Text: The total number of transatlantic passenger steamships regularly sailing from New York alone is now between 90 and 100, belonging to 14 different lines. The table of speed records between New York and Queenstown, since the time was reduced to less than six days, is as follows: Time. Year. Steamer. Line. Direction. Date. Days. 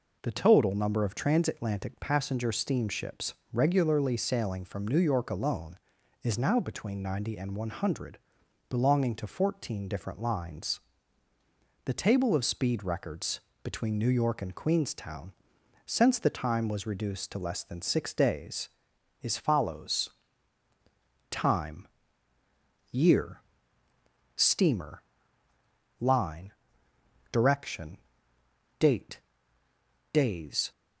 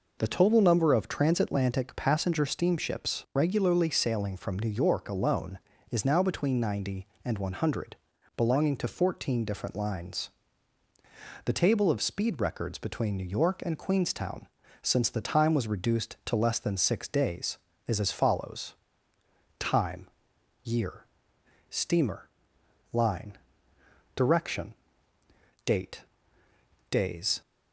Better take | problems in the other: second | pauses between "steamships" and "regularly"; slight; at 3.3 s; 0.20 s long // pauses between "records" and "between"; slight; at 13.3 s; 0.24 s long // skips "as"; at 19.3 s

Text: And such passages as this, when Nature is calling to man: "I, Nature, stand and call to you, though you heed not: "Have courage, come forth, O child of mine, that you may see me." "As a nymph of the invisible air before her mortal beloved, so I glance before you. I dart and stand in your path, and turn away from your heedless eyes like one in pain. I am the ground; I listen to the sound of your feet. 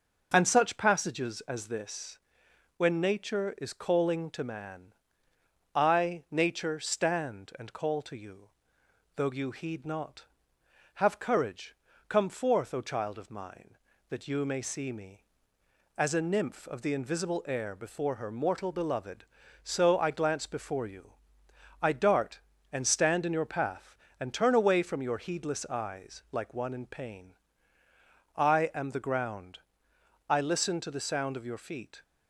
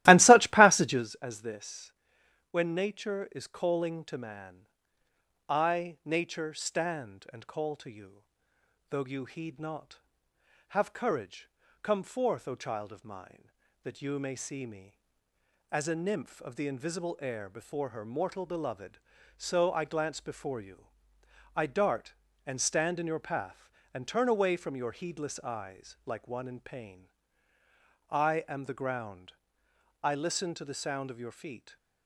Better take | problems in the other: first | starts louder than the rest; strong; until 1.1 s; 16 dB

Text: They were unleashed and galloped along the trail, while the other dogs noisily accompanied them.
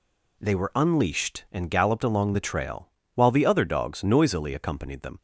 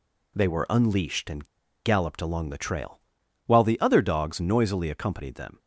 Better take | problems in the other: first | pauses between "and" and "galloped"; at 1.4 s; 0.37 s long

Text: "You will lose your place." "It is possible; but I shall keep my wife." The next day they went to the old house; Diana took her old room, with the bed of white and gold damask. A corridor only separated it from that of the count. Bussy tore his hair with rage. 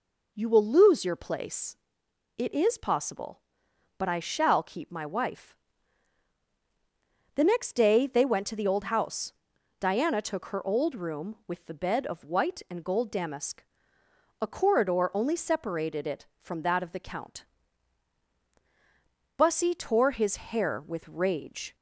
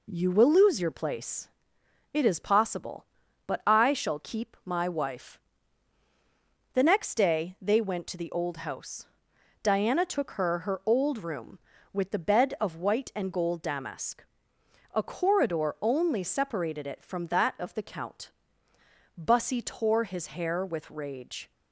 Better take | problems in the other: first | says "her" twice; at 10.5 s

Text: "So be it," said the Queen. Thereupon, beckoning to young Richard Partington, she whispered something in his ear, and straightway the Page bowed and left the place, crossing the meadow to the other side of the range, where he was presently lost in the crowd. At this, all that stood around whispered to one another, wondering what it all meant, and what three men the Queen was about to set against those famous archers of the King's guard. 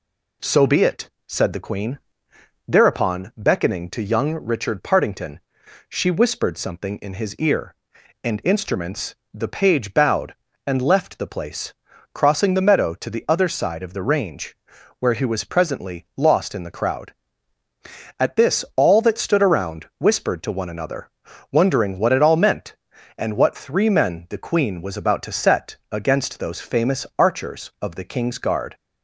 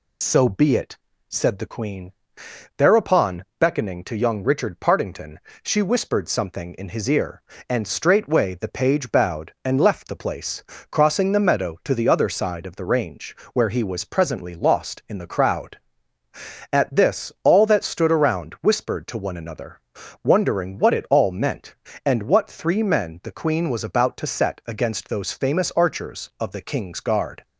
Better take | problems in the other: second | says "instruments" for "straightway"; at 8.4 s

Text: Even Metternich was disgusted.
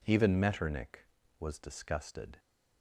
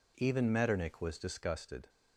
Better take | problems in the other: neither | none

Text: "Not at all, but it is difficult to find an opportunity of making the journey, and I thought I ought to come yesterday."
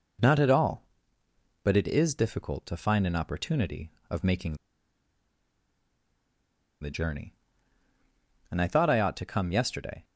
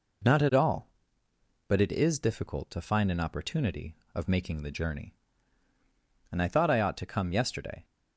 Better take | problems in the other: second | pauses between "making" and "the"; strong; at 4.5 s; 2.2 s long

